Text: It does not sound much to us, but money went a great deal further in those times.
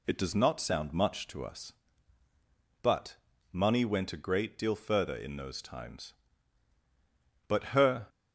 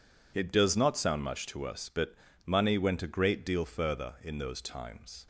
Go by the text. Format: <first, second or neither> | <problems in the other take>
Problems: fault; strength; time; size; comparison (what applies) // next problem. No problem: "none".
second | pauses between "but" and "money"; slight; at 3.1 s; 0.36 s long; slight in the second // goes on to say "But her"; from 7.4 s on; 0.60 s long